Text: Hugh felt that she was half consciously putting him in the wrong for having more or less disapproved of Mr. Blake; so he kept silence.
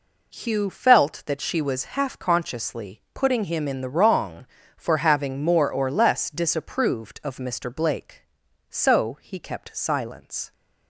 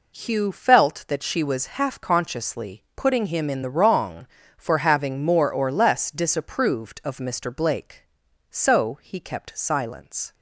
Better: neither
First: none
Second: none

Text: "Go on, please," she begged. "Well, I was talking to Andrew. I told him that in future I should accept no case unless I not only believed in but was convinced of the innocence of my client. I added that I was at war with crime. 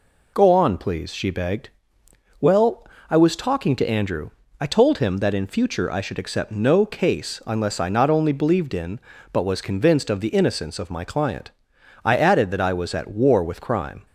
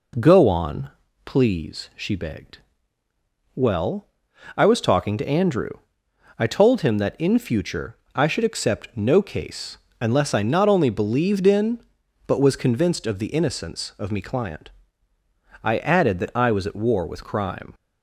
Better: first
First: none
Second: pauses between "future" and "I"; slight; at 7.9 s; 0.18 s long // pauses between "case" and "unless"; slight; at 9.7 s; 0.24 s long // says "me" for "my"; at 14.1 s

